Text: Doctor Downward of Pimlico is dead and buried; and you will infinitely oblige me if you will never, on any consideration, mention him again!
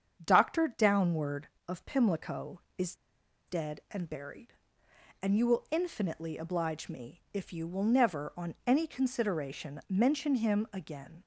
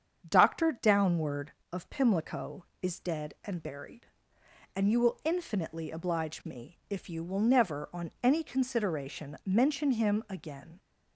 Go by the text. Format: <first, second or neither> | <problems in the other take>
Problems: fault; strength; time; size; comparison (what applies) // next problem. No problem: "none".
second | starts louder than the rest; strong; until 1.2 s; 7.5 dB; strong in the second // pauses between "is" and "dead"; noticeable; at 2.9 s; 0.52 s long